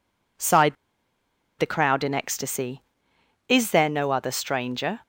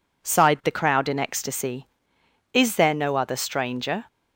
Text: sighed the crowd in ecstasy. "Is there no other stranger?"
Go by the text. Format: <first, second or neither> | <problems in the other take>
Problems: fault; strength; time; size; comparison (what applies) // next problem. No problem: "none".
second | pauses between "sighed" and "the"; noticeable; at 0.7 s; 0.83 s long